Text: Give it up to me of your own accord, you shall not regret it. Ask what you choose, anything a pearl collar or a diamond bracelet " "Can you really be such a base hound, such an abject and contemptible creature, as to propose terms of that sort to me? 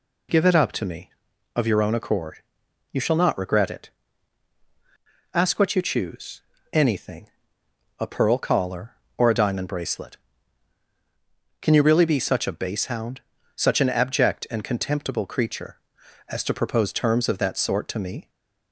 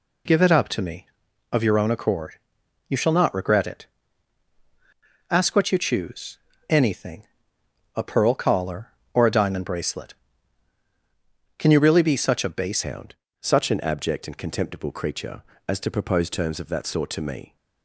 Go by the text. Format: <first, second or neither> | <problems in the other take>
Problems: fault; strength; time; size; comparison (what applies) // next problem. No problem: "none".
first | pauses between "anything" and "a"; noticeable; at 7.2 s; 0.72 s long; noticeable in the first // changes voice at "hound"; from 12.8 s on; 4.7 s long